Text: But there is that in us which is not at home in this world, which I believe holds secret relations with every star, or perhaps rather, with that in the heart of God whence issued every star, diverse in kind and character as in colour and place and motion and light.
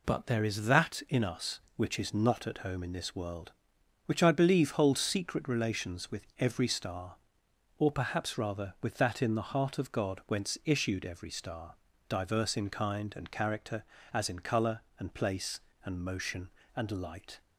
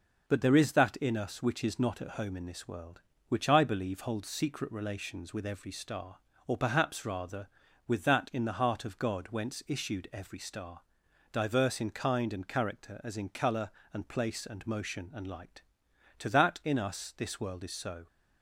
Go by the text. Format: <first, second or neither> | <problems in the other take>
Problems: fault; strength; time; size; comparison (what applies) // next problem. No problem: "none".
first | goes on to say "To that in us this world is so"; strong; from 16.2 s on; 1.8 s long